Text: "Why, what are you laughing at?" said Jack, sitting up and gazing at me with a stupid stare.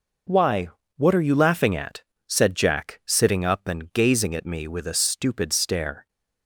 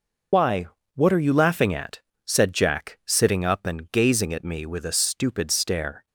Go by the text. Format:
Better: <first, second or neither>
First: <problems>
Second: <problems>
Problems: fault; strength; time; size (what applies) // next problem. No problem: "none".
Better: first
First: none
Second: loses the start of "Why"; at 0.3 s; 80 ms